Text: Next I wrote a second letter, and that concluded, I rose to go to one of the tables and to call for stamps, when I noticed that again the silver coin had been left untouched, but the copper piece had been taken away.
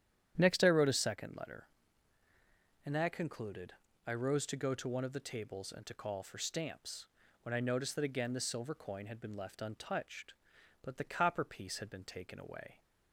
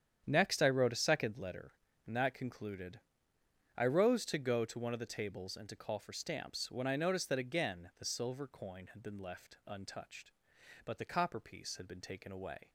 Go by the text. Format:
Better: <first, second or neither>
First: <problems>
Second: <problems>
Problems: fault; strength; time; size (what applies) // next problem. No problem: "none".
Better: neither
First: starts louder than the rest; strong; until 1.4 s; 10.5 dB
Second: starts louder than the rest; strong; until 1.2 s; 9 dB